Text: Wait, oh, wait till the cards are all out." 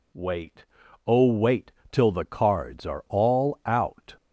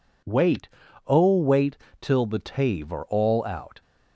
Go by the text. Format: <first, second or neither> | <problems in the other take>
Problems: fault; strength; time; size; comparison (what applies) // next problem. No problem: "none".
first | pauses between "wait" and "till"; slight; at 1.7 s; 0.24 s long; slight in the first // says "tave" for "cards"; at 2.3 s